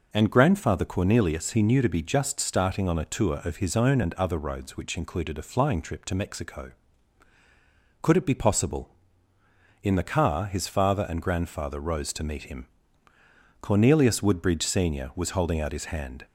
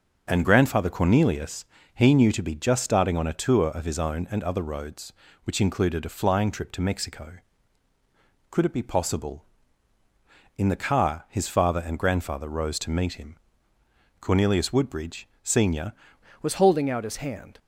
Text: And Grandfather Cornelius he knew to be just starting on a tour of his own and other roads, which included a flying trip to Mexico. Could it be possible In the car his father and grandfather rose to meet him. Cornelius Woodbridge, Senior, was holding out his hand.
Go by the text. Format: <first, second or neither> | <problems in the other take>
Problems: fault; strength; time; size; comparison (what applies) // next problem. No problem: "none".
first | starts louder than the rest; until 1.3 s; 6 dB // pauses between "Cornelius" and "he"; slight; at 1.6 s; 0.30 s long // changes voice at "was"; from 16.4 s on; 1.1 s long